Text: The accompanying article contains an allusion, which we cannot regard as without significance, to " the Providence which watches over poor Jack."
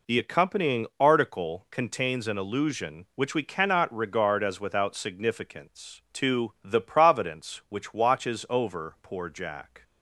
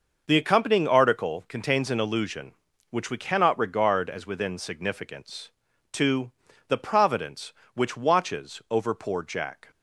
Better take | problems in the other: first | says "within" for "without"; at 4.2 s

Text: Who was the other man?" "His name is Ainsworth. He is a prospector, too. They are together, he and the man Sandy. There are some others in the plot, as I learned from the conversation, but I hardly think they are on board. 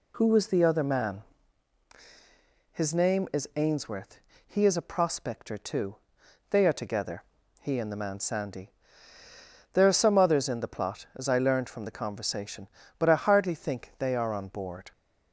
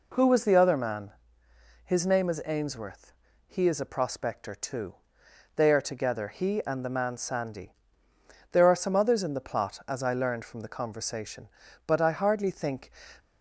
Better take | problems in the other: first | stops before "they are on board"; at 13.1 s

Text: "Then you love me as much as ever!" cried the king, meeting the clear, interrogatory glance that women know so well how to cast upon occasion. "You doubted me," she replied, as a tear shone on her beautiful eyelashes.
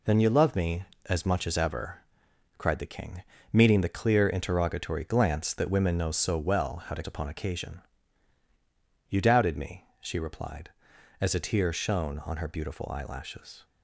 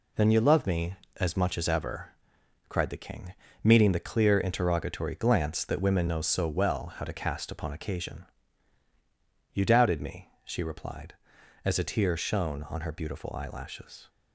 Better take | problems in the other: second | skips "cast"; at 7.0 s

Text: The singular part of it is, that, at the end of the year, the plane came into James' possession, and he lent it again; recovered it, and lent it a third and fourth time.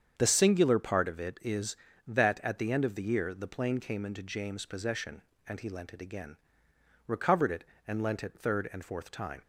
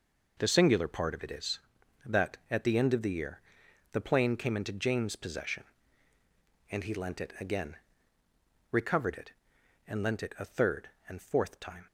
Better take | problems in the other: second | starts louder than the rest; strong; until 1.1 s; 7.5 dB // skips "a"; at 8.3 s

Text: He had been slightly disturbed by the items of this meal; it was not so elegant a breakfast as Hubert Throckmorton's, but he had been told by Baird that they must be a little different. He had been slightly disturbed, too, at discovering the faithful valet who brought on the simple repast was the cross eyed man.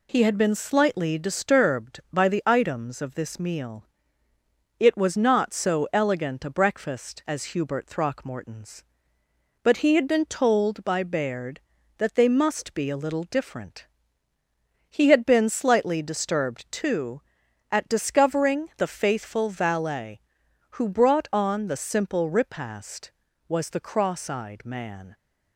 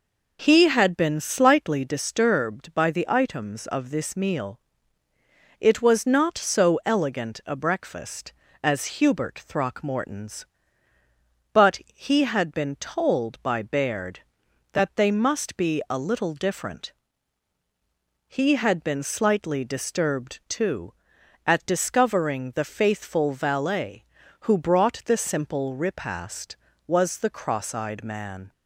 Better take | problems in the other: first | skips "on"; at 25.0 s

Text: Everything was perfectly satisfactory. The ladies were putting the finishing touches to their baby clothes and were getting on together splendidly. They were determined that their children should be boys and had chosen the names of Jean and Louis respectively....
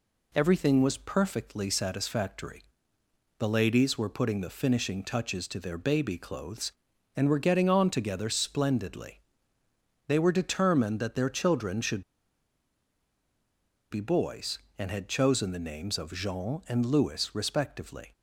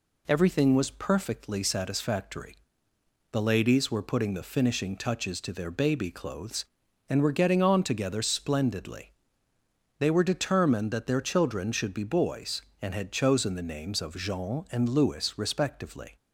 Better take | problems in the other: second | pauses between "should" and "be"; strong; at 12.0 s; 1.8 s long

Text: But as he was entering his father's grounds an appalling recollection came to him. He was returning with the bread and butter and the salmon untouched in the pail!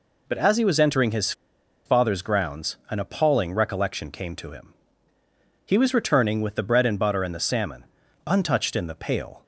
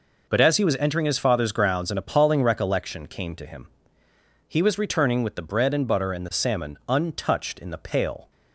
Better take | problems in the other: second | pauses between "his" and "father's"; noticeable; at 1.3 s; 0.53 s long // pauses between "salmon" and "untouched"; at 7.8 s; 0.42 s long

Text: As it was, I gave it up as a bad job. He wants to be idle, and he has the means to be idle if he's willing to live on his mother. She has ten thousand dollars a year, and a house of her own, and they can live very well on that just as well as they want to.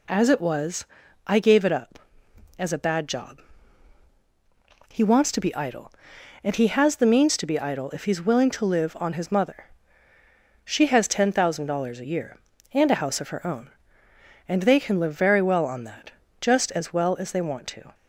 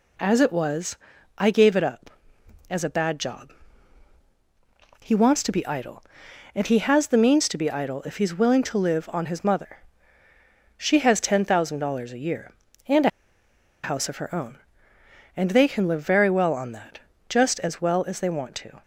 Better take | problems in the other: first | pauses between "a" and "house"; noticeable; at 13.0 s; 0.73 s long // pauses between "that" and "just"; slight; at 16.9 s; 0.28 s long; slight in the first

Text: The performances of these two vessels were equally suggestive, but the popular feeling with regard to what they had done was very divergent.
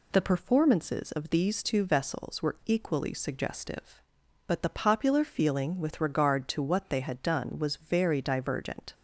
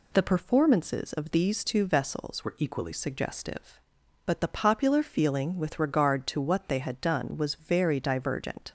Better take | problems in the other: first | changes voice from "were" to "equally"; from 2.4 to 2.9 s; 0.5 s long

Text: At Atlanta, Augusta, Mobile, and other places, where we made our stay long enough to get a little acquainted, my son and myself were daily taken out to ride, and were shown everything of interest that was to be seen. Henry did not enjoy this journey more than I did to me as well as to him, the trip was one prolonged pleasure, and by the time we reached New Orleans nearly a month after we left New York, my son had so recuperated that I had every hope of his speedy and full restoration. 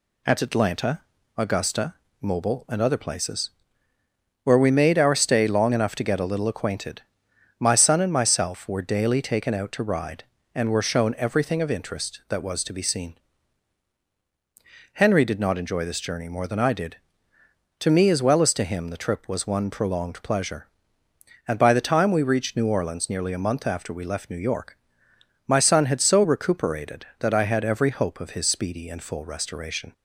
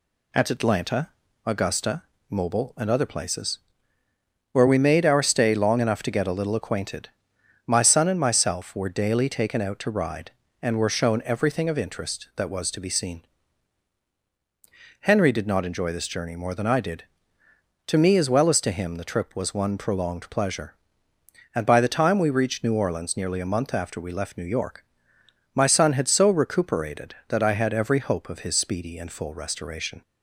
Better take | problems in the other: neither | none

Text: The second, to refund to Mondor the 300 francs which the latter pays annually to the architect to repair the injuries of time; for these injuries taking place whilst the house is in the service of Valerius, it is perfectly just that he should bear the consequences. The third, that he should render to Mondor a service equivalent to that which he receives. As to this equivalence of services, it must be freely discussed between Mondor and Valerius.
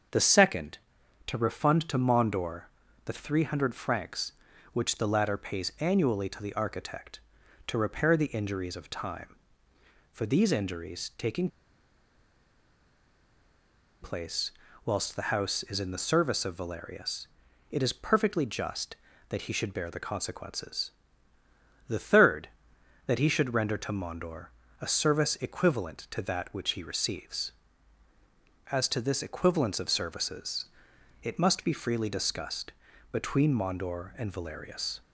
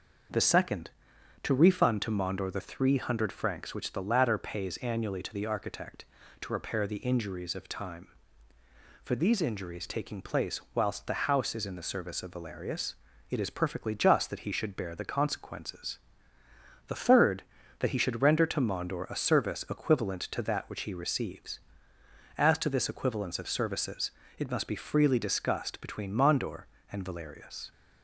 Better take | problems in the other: second | starts louder than the rest; until 1.6 s; 6.5 dB // pauses between "Mondor" and "the"; at 2.6 s; 0.42 s long // pauses between "taking" and "place"; strong; at 11.4 s; 2.5 s long // pauses between "place" and "whilst"; slight; at 14.5 s; 0.34 s long // pauses between "Mondor" and "a"; slight; at 24.4 s; 0.34 s long // pauses between "discussed" and "between"; at 32.7 s; 0.40 s long

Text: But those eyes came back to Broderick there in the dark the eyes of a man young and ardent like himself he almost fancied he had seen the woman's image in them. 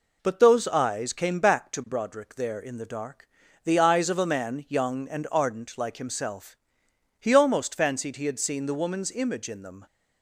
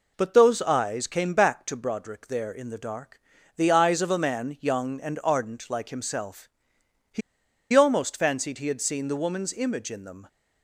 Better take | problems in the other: first | pauses between "dark" and "the"; slight; at 3.1 s; 0.36 s long; slight in the first // pauses between "himself" and "he"; noticeable; at 6.4 s; 0.64 s long; noticeable in the first // pauses between "he" and "almost"; noticeable; at 7.2 s; 0.52 s long

